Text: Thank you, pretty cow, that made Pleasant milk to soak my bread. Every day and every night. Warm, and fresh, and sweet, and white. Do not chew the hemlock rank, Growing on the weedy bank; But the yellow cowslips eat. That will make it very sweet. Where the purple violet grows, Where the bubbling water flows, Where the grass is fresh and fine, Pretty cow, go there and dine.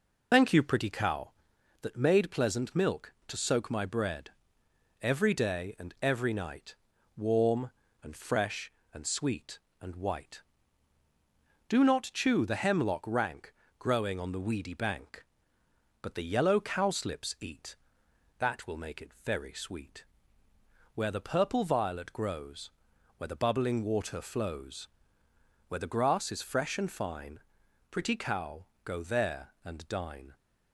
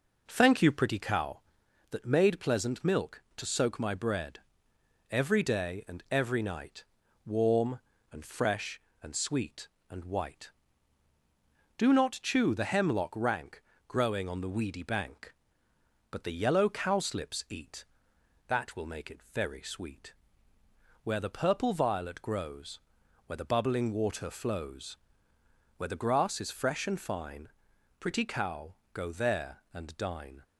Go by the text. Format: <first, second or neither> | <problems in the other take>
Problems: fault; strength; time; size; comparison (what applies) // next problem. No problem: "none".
second | loses the start of "Thank"; at 0.3 s; 140 ms